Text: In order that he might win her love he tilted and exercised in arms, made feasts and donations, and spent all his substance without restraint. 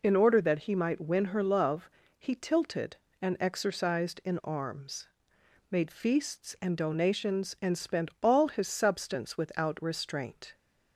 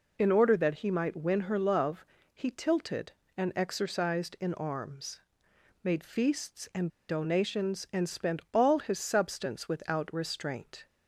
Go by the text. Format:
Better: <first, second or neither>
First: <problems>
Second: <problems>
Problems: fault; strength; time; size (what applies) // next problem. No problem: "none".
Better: first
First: pauses between "love" and "he"; slight; at 1.8 s; 0.30 s long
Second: pauses between "love" and "he"; slight; at 2.0 s; 0.30 s long // pauses between "and" and "donations"; slight; at 6.8 s; 0.21 s long